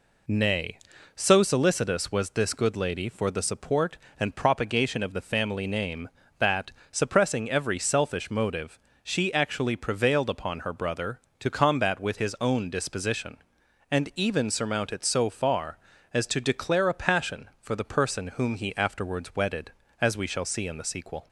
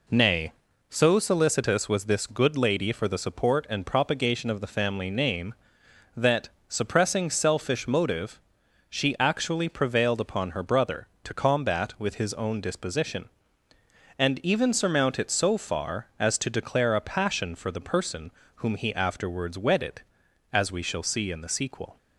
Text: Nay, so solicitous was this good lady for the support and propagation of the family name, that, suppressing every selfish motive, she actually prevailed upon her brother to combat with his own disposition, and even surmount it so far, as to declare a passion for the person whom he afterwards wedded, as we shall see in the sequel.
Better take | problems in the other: first | skips "every"; at 7.2 s // pauses between "person" and "whom"; slight; at 18.3 s; 0.26 s long

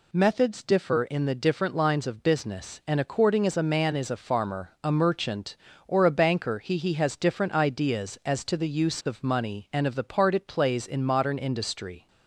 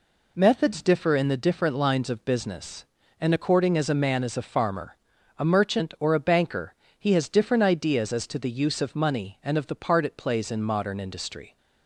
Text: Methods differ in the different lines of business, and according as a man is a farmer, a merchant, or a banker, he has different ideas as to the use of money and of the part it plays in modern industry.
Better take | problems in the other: second | says "he" twice; at 6.7 s

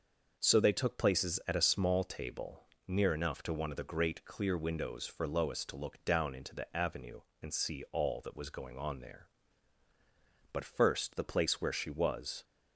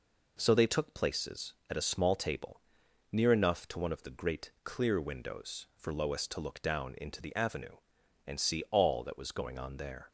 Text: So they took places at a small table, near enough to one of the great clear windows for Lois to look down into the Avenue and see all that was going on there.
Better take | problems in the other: second | goes on to say "But first the place where she was"; strong; from 10.5 s on; 1.9 s long

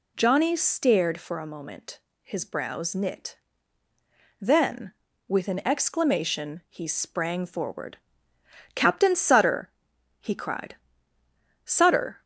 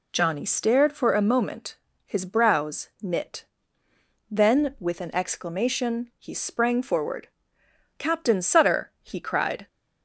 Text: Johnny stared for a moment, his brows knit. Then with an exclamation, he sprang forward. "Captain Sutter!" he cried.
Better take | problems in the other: second | goes on to say "Sutter"; from 11.6 s on; 0.58 s long

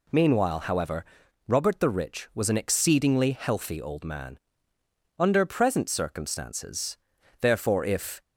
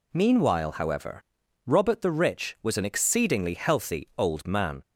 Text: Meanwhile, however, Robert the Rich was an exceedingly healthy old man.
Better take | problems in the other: second | goes on to say "Under present circumstances therefore if"; strong; from 5.1 s on; 3.0 s long

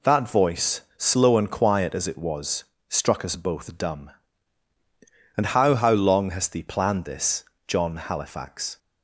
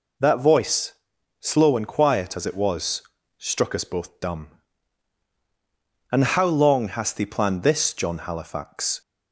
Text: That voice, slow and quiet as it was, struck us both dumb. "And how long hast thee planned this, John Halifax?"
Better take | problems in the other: second | says "how" twice; at 5.7 s

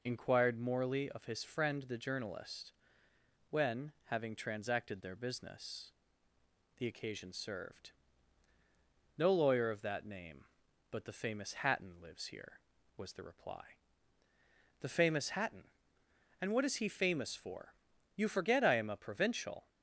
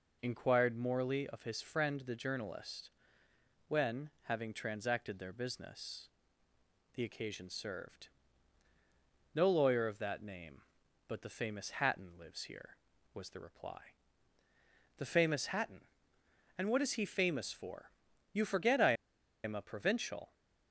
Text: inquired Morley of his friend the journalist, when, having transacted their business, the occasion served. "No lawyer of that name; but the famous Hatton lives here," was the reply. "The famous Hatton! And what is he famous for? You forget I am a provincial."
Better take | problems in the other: first | pauses between "I" and "am"; noticeable; at 18.9 s; 0.53 s long

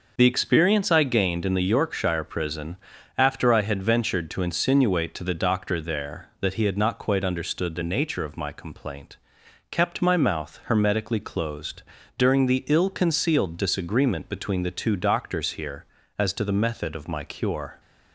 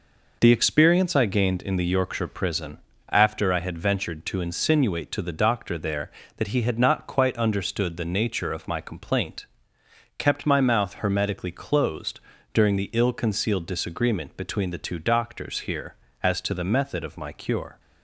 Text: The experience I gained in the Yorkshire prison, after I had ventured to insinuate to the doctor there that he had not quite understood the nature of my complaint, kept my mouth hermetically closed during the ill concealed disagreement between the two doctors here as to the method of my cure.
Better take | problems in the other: neither | pauses between "closed" and "during"; slight; the same in both

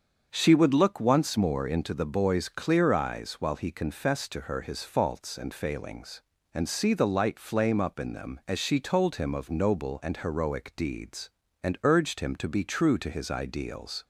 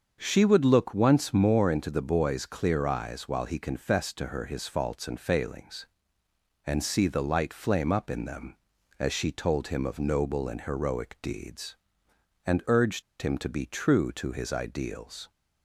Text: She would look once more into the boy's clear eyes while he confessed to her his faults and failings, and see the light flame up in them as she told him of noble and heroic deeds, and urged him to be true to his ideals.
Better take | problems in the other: first | starts louder than the rest; until 1.2 s; 7 dB; strong in the first // pauses between "urged" and "him"; slight; at 13.0 s; 0.19 s long

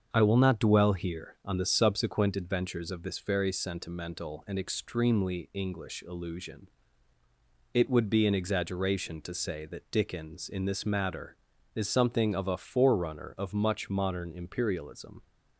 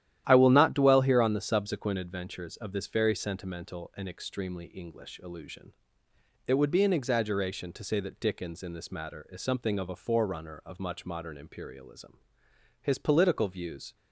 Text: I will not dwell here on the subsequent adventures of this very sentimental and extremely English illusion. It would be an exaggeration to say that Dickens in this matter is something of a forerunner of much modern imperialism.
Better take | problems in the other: first | starts louder than the rest; strong; until 1.2 s; 12 dB; also in the first // goes on to say "His political views"; noticeable; from 12.8 s on; 1.1 s long

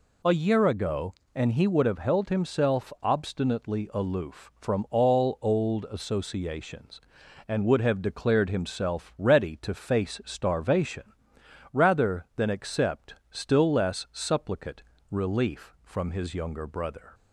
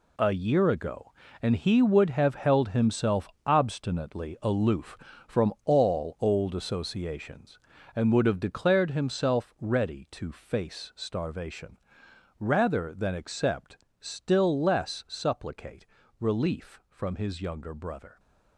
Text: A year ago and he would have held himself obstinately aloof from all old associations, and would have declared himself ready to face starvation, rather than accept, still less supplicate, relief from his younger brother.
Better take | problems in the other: first | gets quieter; strong; throughout; 10.5 dB // pauses between "himself" and "obstinately"; slight; at 3.2 s; 0.20 s long

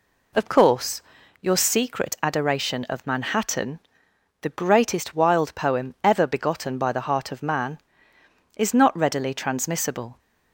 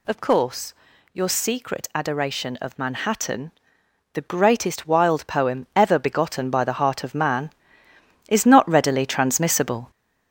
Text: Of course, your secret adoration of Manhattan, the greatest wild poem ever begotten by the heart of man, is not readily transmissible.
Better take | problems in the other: first | gets louder; noticeable; throughout; 5.5 dB

